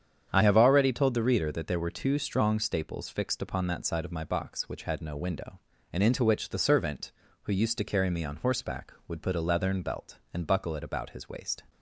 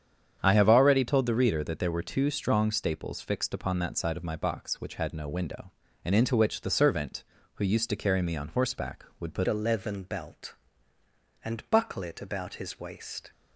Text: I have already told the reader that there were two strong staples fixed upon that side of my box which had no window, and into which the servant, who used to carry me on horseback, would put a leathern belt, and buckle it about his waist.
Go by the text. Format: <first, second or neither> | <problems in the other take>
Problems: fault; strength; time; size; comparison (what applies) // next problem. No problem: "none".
first | starts louder than the rest; strong; until 1.4 s; 8 dB; strong in the first // changes voice at "a"; from 9.4 s on; 3.9 s long